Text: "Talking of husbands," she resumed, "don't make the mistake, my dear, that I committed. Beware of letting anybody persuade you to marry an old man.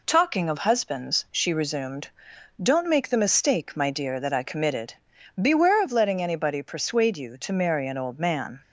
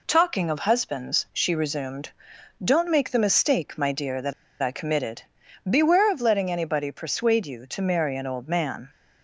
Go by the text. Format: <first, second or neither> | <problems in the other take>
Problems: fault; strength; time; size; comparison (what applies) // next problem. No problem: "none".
first | pauses between "that" and "I"; slight; at 4.3 s; 0.28 s long